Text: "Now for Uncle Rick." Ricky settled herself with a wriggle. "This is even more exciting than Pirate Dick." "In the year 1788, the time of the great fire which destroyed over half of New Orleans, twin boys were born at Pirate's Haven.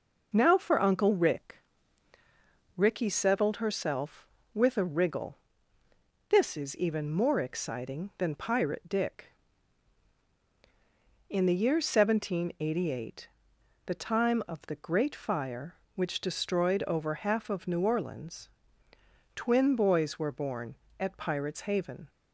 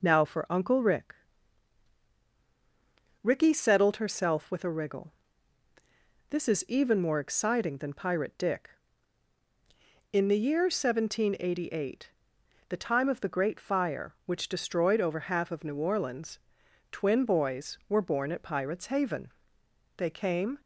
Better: first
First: none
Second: goes on to say "They came"; noticeable; from 19.9 s on; 0.62 s long

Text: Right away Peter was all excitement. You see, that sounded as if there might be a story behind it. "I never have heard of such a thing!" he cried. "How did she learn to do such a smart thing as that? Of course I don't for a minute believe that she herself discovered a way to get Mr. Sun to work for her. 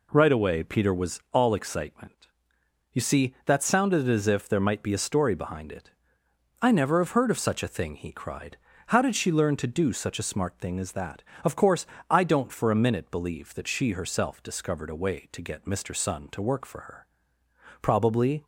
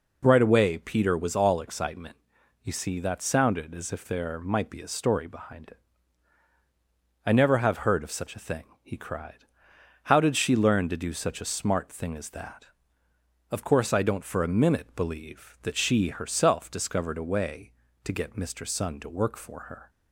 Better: second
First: pauses between "course" and "I"; slight; at 11.8 s; 0.24 s long // goes on to say "Probably"; noticeable; from 17.8 s on; 0.62 s long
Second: none

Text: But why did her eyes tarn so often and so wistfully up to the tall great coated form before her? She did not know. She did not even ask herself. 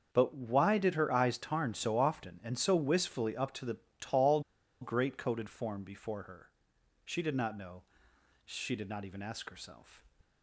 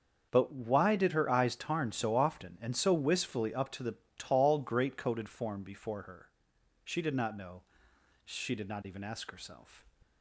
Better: second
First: starts louder than the rest; until 1.1 s; 6.5 dB // pauses between "the" and "tall"; slight; at 3.7 s; 0.22 s long // pauses between "tall" and "great"; at 4.4 s; 0.40 s long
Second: starts louder than the rest; until 1.3 s; 6.5 dB // pauses between "the" and "tall"; slight; at 3.9 s; 0.22 s long

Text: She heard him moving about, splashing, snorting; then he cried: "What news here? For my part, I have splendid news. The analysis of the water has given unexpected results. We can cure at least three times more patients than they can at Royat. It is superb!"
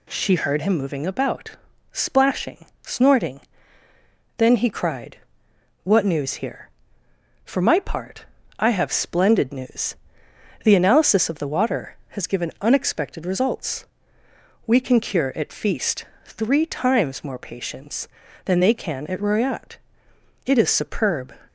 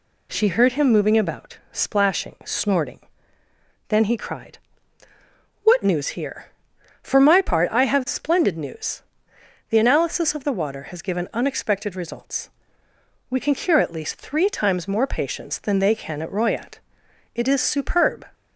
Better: second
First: says "feast" for "least"; at 15.5 s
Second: none

